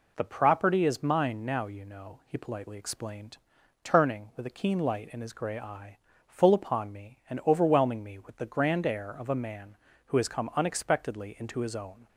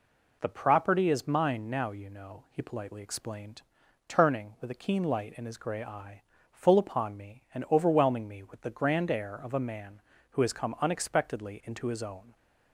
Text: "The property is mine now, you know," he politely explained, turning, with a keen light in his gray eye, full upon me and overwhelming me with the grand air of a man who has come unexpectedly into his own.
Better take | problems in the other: neither | none

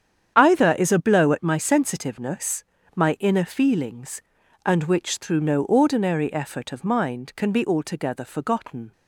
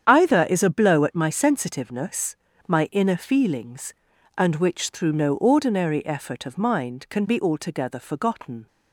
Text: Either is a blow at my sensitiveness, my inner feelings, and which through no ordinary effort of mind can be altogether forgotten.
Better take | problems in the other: neither | starts louder than the rest; strong; the same in both

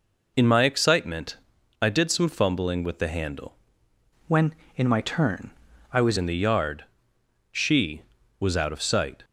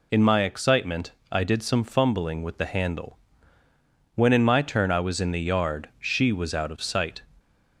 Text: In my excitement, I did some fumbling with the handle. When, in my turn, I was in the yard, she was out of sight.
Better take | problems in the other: second | changes voice from "When" to "was"; from 4.2 to 6.1 s; 1.9 s long

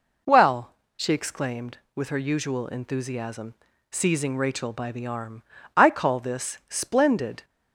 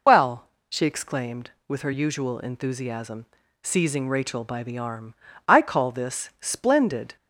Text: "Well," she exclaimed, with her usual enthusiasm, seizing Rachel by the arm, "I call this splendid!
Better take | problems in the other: first | loses the start of "Well"; at 0.0 s; 55 ms

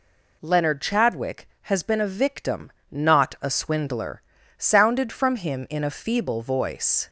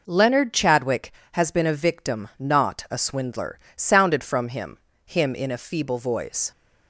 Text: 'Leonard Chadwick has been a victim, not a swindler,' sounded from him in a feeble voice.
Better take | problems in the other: first | says "him" twice; at 5.0 s

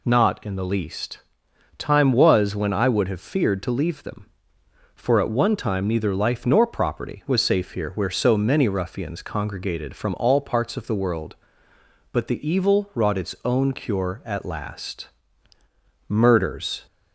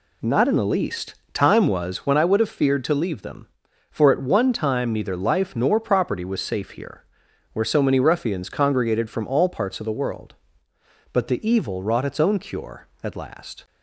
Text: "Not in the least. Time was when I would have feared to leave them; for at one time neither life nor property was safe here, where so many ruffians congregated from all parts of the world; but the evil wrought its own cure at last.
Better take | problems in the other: second | goes on to say "Murders"; noticeable; from 16.0 s on; 0.78 s long

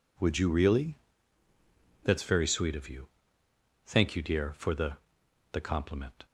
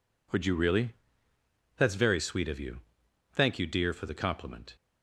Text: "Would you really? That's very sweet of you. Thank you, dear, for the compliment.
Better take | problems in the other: second | says "the" twice; at 5.5 s

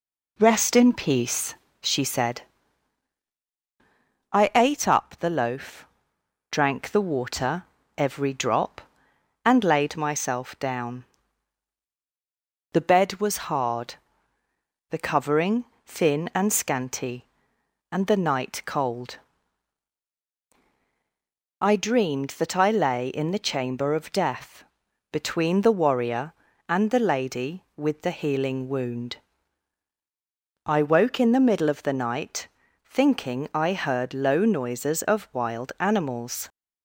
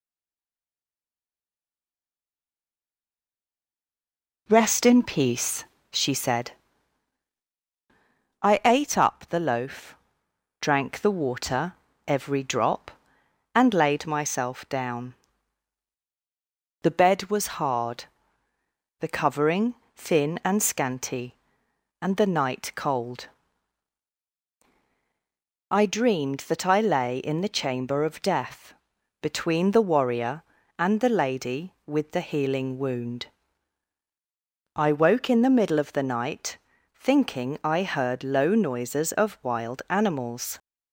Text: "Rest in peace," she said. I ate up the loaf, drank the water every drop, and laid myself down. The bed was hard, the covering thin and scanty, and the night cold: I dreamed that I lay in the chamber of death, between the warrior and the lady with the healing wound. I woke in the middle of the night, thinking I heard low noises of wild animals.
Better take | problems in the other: first | stays silent before the first word; strong; until 4.4 s; 4.4 s long // pauses between "water" and "every"; slight; at 11.7 s; 0.32 s long; slight in the first // pauses between "covering" and "thin"; slight; at 19.7 s; 0.22 s long; slight in the first

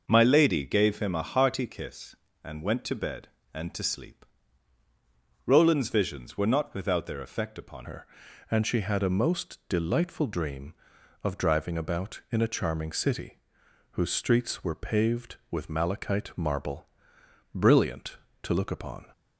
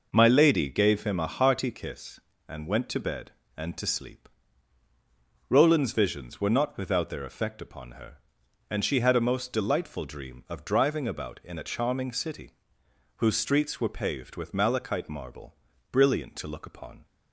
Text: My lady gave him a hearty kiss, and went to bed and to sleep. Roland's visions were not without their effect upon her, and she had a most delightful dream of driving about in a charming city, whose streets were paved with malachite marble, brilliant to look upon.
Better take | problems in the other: second | changes voice at "her"; from 7.8 s on; 11.2 s long

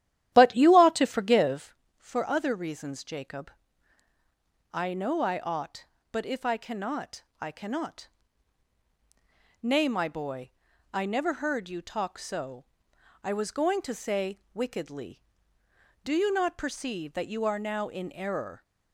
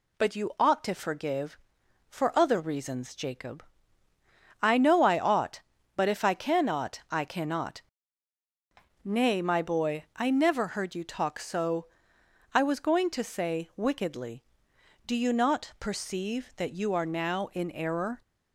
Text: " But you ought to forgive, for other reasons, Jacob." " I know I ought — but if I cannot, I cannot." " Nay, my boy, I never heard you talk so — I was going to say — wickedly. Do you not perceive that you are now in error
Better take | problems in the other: second | starts louder than the rest; strong; until 1.8 s; 13 dB

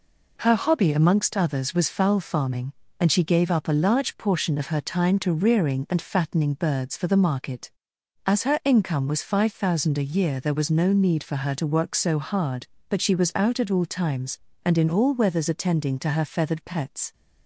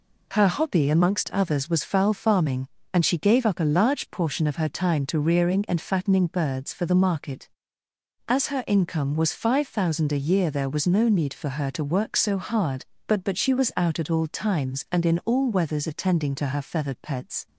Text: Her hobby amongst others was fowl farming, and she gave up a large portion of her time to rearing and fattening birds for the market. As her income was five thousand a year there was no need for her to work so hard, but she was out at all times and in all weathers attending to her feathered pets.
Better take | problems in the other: first | says "but" twice; at 13.2 s

